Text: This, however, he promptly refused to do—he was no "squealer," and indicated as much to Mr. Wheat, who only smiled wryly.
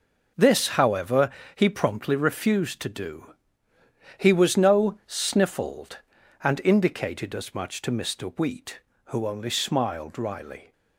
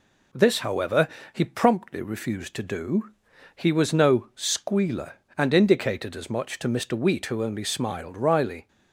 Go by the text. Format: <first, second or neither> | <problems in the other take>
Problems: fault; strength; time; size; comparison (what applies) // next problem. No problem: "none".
second | says "sniffled" for "squealer"; at 5.0 s